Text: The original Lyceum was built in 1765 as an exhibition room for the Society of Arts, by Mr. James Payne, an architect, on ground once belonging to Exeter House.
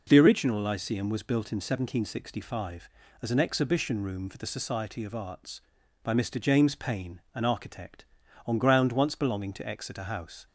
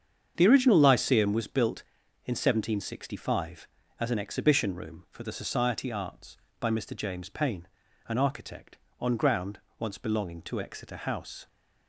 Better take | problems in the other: first | starts louder than the rest; strong; until 1.3 s; 7.5 dB // skips "of"; at 5.9 s // pauses between "ground" and "once"; slight; at 9.5 s; 0.20 s long

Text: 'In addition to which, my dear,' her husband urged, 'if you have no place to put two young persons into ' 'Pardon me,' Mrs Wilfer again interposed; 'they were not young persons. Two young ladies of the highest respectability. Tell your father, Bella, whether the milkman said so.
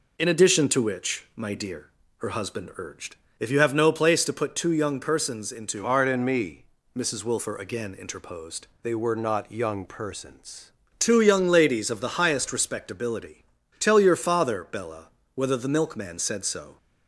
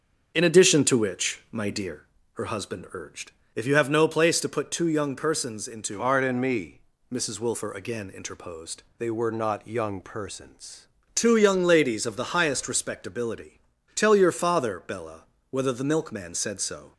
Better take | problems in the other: first | starts louder than the rest; until 2.2 s; 6.5 dB

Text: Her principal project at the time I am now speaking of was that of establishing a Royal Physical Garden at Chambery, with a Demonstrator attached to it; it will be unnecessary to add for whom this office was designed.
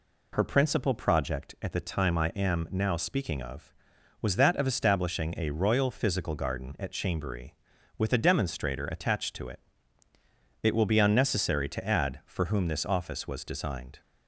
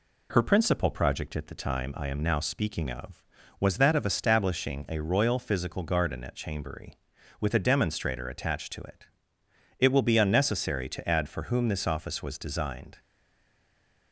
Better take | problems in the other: first | stays silent after the last word; from 12.9 s on; 1.2 s long

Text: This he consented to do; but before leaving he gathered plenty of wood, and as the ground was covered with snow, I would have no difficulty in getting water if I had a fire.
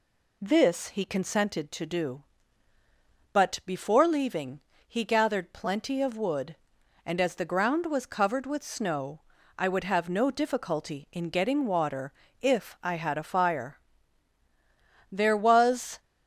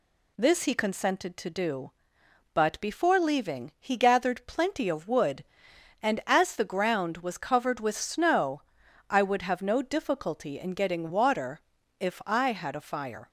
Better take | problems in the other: second | pauses between "leaving" and "he"; slight; at 4.5 s; 0.26 s long // pauses between "water" and "if"; slight; at 12.1 s; 0.30 s long; also in the second // goes on to say "There was"; noticeable; from 15.0 s on; 0.90 s long

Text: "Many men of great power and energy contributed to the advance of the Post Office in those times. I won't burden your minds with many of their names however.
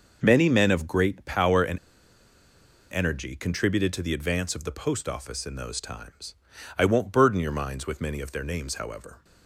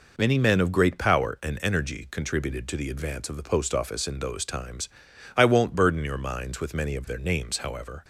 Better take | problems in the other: second | pauses between "and" and "energy"; at 1.7 s; 1.1 s long

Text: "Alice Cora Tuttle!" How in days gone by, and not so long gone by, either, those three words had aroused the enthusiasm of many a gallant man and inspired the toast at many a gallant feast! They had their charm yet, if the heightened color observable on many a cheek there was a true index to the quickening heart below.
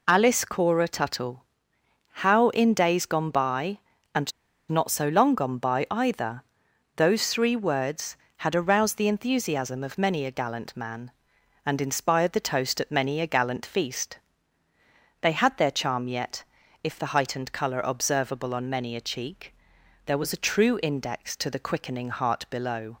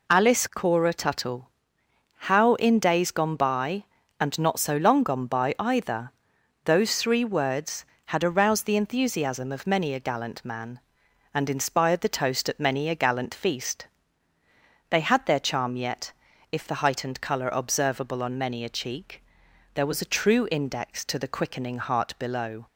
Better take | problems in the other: second | pauses between "and" and "not"; at 4.3 s; 0.38 s long // pauses between "cheek" and "there"; noticeable; at 19.5 s; 0.50 s long; noticeable in the second

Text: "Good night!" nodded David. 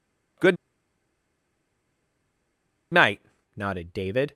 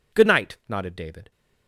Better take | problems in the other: second | pauses between "Good" and "night"; strong; at 0.5 s; 2.3 s long

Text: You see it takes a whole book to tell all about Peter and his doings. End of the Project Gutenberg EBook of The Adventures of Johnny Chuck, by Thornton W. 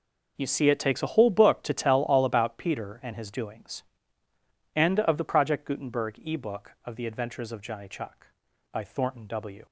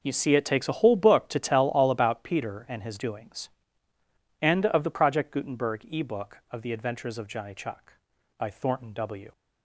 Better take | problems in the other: neither | none

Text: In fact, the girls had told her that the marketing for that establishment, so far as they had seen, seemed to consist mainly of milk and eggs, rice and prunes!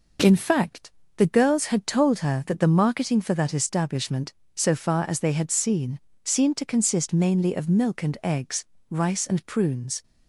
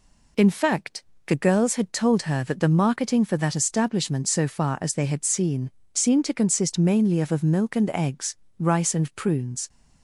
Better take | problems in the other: first | says "of" twice; at 7.3 s

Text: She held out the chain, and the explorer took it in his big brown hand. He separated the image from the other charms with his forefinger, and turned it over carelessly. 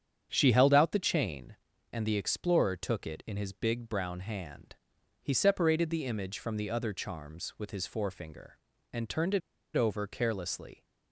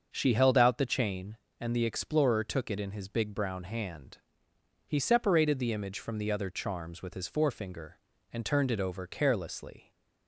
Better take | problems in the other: second | starts louder than the rest; strong; until 1.3 s; 8 dB; also in the second // pauses between "it" and "over"; slight; at 9.4 s; 0.35 s long

